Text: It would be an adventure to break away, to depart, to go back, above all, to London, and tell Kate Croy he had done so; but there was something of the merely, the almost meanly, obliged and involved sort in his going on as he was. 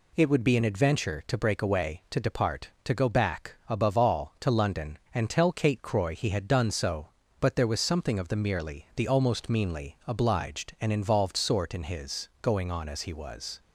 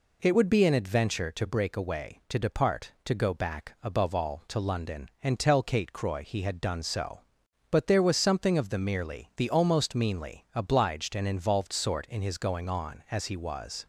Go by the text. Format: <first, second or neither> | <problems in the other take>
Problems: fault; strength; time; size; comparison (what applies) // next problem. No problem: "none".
neither | none